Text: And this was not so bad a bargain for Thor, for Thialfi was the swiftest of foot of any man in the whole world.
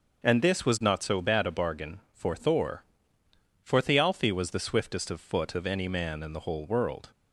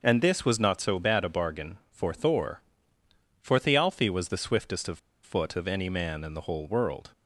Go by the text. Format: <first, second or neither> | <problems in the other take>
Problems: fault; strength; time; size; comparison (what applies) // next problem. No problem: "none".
first | pauses between "of" and "foot"; slight; at 4.9 s; 0.25 s long